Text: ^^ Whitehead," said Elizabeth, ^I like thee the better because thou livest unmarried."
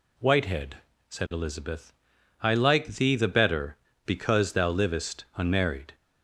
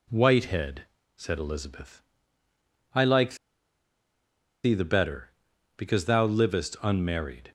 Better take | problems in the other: first | pauses between "like" and "thee"; strong; at 3.3 s; 1.2 s long

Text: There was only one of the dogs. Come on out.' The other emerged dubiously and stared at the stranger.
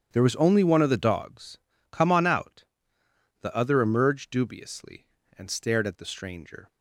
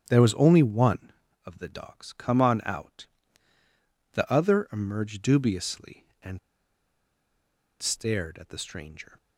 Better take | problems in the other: first | starts louder than the rest; strong; until 1.0 s; 8.5 dB; strong in the first // pauses between "and" and "stared"; strong; at 6.3 s; 1.4 s long

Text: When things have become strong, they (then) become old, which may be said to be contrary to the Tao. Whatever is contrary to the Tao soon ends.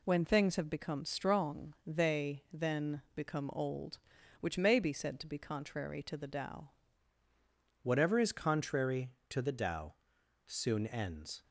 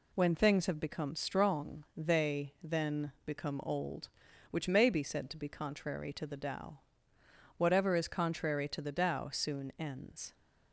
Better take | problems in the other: second | changes voice at "Whatever"; from 7.8 s on; 3.6 s long // pauses between "Tao" and "soon"; noticeable; at 9.9 s; 0.50 s long

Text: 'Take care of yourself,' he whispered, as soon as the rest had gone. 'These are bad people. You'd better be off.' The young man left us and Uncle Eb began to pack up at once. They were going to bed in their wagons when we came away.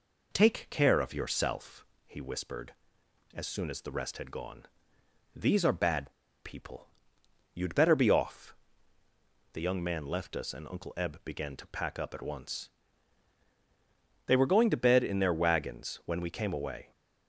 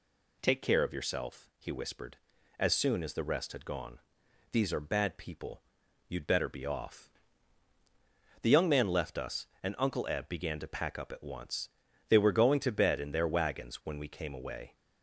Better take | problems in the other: second | pauses between "bad" and "people"; slight; at 6.1 s; 0.33 s long

